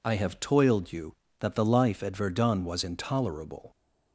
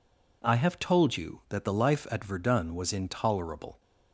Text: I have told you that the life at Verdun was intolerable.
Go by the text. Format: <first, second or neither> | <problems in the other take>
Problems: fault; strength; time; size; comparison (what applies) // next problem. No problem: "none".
second | says "toiled" for "told"; at 0.4 s